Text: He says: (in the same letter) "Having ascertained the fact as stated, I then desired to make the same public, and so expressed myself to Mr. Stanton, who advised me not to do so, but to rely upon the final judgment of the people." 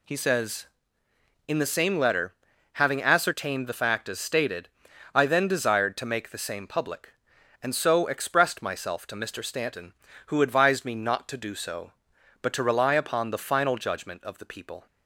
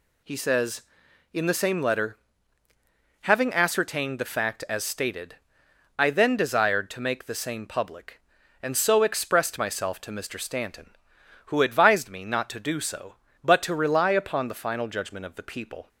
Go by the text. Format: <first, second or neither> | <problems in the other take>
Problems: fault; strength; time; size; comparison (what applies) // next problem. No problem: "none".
neither | none